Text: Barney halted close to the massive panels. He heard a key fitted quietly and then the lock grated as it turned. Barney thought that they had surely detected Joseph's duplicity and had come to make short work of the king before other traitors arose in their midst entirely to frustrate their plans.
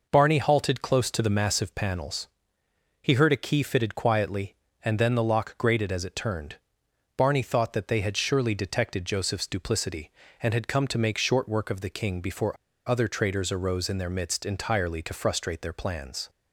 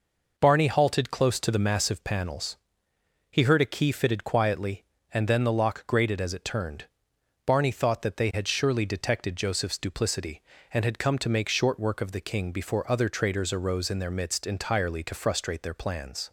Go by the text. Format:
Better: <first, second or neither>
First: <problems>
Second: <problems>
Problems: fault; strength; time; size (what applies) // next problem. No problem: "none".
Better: second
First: pauses between "before" and "other"; slight; at 12.5 s; 0.31 s long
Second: none